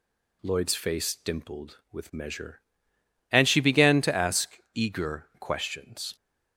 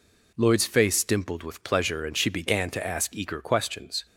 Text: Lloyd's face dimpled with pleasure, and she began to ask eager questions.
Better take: second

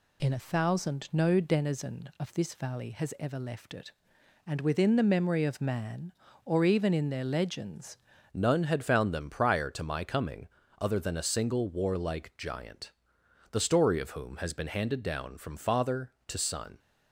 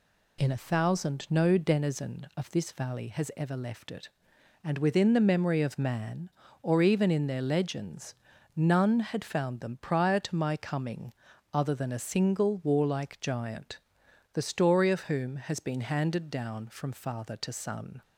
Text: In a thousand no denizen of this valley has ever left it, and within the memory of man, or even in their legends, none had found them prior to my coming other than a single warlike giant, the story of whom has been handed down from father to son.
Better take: second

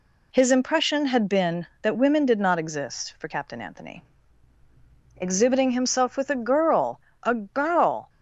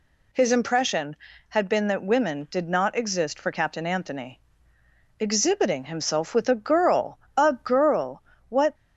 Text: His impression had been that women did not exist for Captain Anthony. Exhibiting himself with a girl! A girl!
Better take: first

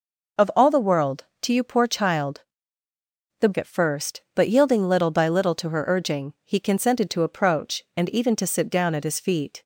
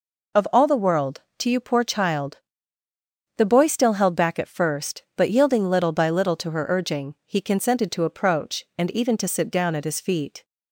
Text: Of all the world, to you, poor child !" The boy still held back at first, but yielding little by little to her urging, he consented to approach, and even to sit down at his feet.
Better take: second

